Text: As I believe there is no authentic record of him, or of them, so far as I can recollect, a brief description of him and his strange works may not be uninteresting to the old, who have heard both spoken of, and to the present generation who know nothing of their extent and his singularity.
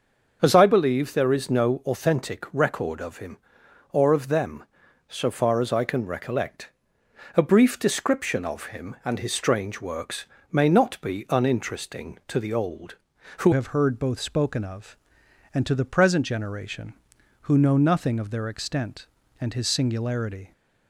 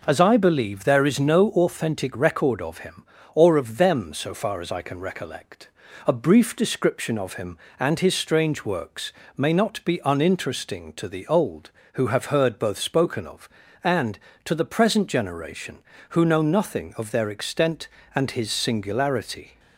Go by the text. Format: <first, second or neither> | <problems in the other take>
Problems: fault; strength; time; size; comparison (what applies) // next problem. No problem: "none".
second | starts louder than the rest; until 1.4 s; 6.5 dB // pauses between "works" and "may"; slight; at 10.2 s; 0.26 s long; slight in the second // changes voice at "have"; from 13.5 s on; 7.0 s long